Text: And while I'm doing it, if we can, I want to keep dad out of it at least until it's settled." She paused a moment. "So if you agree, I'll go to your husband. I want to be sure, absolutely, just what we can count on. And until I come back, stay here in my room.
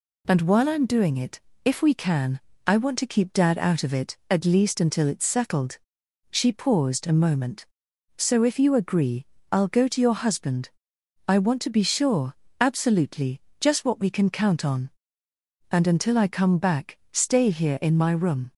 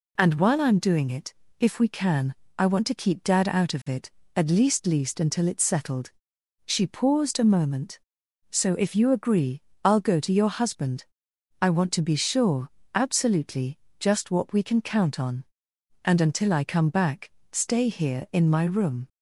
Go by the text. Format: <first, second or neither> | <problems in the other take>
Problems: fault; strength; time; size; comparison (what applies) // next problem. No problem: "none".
first | says "least" twice; at 4.8 s